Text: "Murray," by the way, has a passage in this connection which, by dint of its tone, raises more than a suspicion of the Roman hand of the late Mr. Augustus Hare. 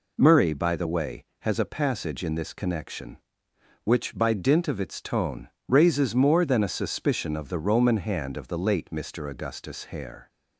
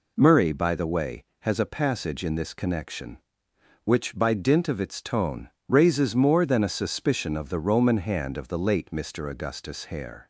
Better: neither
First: none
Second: none

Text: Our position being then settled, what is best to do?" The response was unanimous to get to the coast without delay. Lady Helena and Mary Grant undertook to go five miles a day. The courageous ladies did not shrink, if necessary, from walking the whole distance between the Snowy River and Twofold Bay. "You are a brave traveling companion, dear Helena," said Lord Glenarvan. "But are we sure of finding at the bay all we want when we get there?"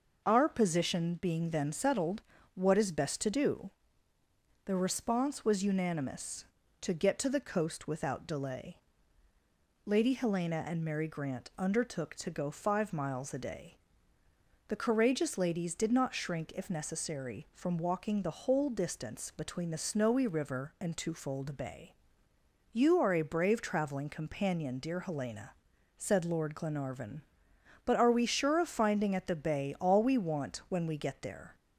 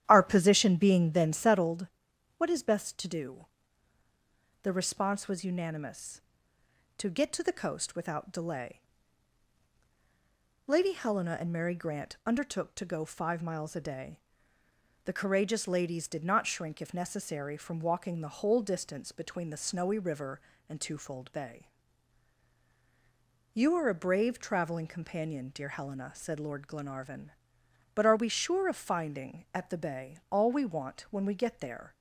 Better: first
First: none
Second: starts louder than the rest; strong; until 1.8 s; 11.5 dB

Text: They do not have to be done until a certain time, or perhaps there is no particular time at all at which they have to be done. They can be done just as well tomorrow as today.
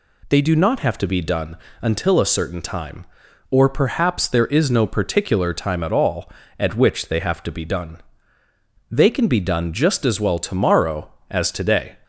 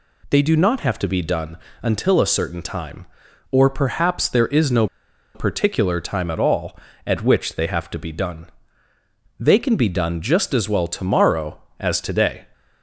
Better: first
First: pauses between "done" and "until"; slight; at 1.5 s; 0.26 s long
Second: pauses between "done" and "until"; slight; at 1.5 s; 0.26 s long // pauses between "no" and "particular"; noticeable; at 4.8 s; 0.47 s long

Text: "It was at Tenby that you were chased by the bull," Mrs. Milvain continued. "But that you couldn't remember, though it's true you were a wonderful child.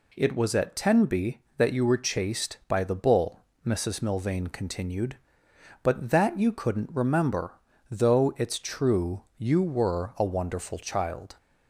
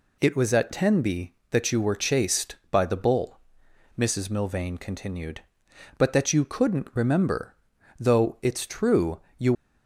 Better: first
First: pauses between "true" and "you"; slight; at 9.2 s; 0.16 s long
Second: pauses between "true" and "you"; slight; at 9.2 s; 0.18 s long // stops before "were a wonderful child"; at 9.5 s

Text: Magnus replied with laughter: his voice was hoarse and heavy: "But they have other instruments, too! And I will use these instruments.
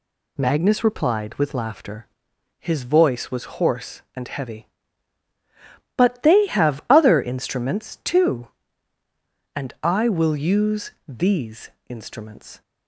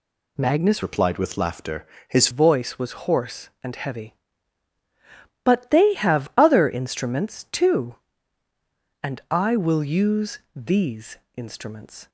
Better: first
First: pauses between "use" and "these"; slight; at 10.8 s; 0.18 s long // pauses between "these" and "instruments"; slight; at 11.6 s; 0.18 s long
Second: changes voice from "replied" to "his"; from 0.8 to 2.2 s; 1.4 s long // pauses between "use" and "these"; slight; at 10.3 s; 0.18 s long // pauses between "these" and "instruments"; slight; at 11.1 s; 0.18 s long

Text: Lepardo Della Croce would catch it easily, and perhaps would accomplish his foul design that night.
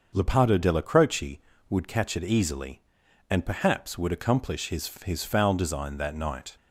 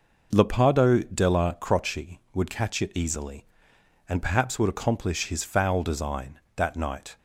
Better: second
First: starts louder than the rest; noticeable; until 1.1 s; 6 dB // says "his" twice; at 5.0 s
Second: none

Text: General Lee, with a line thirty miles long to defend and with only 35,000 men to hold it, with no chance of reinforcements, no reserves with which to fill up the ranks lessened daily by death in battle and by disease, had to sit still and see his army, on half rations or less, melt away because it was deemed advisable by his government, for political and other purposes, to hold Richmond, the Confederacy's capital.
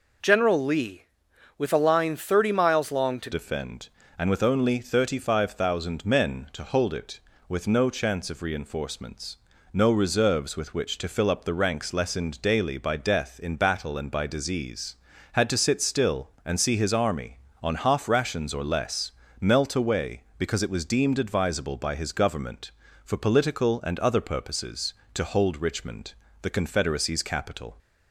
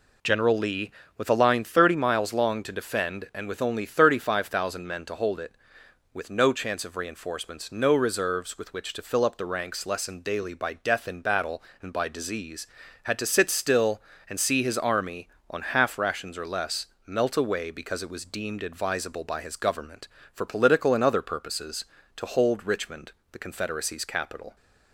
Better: second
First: changes voice at "defend"; from 3.3 s on; 24.4 s long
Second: none

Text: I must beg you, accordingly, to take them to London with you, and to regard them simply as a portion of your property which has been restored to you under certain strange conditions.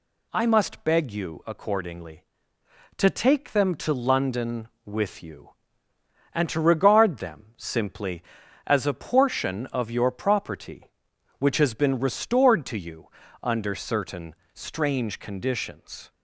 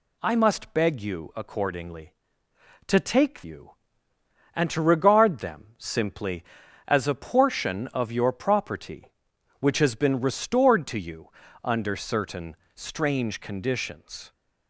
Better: first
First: pauses between "you" and "under"; slight; at 13.0 s; 0.36 s long // pauses between "certain" and "strange"; slight; at 14.3 s; 0.18 s long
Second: skips "them to London with"; at 3.4 s // pauses between "you" and "under"; slight; at 11.2 s; 0.36 s long // pauses between "certain" and "strange"; slight; at 12.5 s; 0.18 s long

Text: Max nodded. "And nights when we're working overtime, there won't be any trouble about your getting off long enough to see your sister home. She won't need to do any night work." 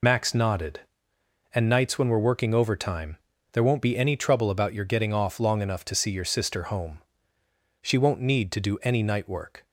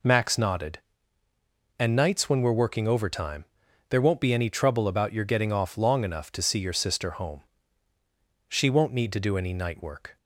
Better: second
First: loses the start of "Max"; at 0.0 s; 40 ms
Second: none

